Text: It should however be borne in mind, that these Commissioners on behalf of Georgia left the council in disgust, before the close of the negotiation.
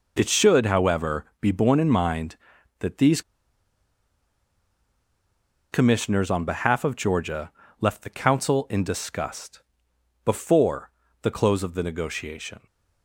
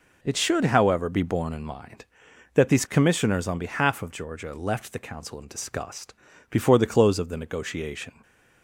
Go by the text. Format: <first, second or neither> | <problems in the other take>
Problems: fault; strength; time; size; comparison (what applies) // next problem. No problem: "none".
second | pauses between "however" and "be"; slight; at 1.2 s; 0.16 s long // pauses between "these" and "Commissioners"; strong; at 3.2 s; 2.5 s long // pauses between "Georgia" and "left"; slight; at 7.5 s; 0.28 s long // pauses between "before" and "the"; slight; at 10.8 s; 0.32 s long